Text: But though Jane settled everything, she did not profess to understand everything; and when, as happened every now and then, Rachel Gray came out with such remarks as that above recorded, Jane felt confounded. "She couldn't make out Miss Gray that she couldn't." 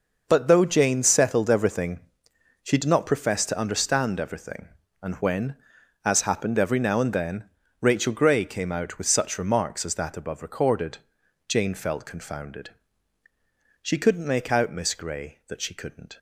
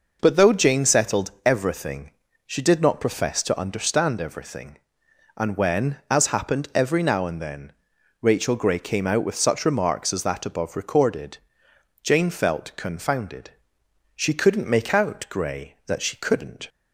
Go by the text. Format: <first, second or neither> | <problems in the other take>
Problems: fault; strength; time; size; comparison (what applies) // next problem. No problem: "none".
first | skips "Miss"; at 15.2 s